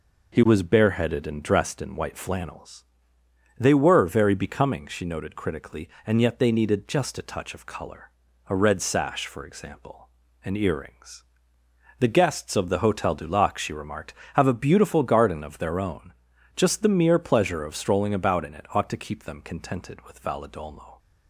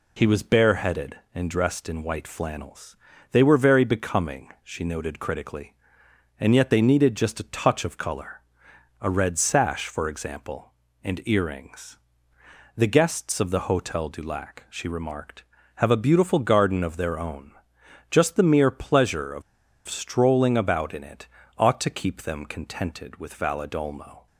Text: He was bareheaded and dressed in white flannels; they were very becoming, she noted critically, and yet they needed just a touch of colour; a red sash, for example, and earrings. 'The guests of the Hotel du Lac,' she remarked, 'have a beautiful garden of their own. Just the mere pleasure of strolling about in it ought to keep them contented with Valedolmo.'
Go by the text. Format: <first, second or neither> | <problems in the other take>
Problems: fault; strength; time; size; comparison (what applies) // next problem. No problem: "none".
first | pauses between "of" and "strolling"; noticeable; at 19.4 s; 0.45 s long // pauses between "it" and "ought"; slight; at 21.2 s; 0.30 s long